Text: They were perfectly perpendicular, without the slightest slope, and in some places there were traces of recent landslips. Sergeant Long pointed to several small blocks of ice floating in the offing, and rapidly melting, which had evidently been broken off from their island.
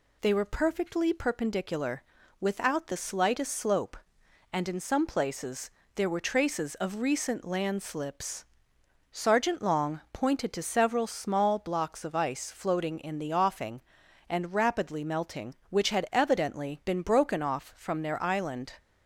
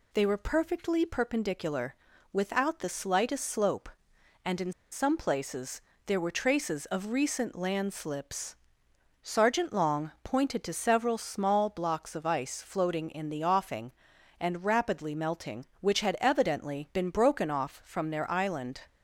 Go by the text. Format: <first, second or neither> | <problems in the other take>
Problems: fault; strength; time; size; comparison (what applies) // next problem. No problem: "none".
first | pauses between "in" and "some"; slight; at 4.7 s; 0.20 s long // pauses between "places" and "there"; slight; at 5.7 s; 0.26 s long; slight in the first